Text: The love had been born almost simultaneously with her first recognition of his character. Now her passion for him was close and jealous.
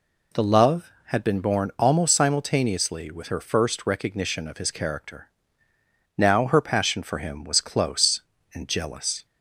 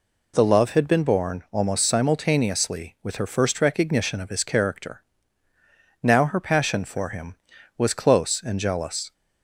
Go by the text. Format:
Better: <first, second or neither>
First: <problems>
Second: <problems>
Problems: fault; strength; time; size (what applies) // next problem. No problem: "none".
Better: neither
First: none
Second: none